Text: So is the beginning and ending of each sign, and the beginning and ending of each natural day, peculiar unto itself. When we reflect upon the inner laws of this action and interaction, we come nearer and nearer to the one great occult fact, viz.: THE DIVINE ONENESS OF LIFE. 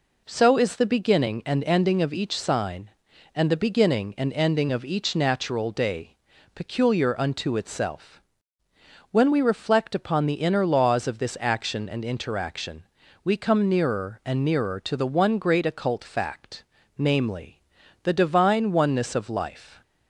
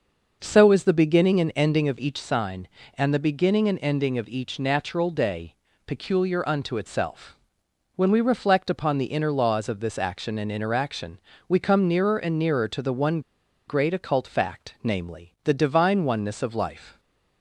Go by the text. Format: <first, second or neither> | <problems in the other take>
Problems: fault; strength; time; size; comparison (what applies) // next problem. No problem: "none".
first | starts louder than the rest; noticeable; until 1.4 s; 6 dB // pauses between "one" and "great"; noticeable; at 13.1 s; 0.48 s long